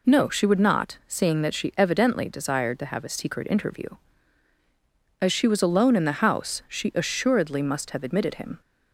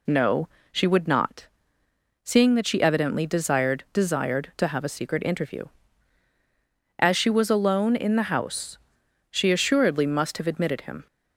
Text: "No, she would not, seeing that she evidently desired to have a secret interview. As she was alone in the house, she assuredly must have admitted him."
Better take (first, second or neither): first